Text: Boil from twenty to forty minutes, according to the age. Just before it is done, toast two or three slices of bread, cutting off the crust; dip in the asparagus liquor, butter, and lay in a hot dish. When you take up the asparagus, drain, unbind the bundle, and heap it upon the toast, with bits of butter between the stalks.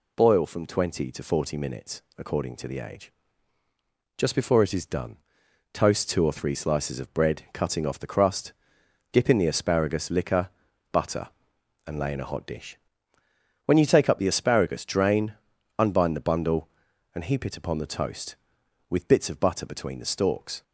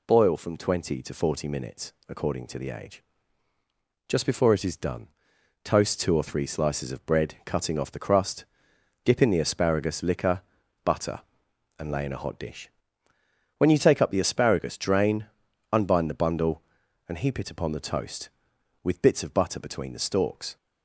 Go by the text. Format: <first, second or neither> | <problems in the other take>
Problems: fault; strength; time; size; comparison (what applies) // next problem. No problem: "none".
neither | none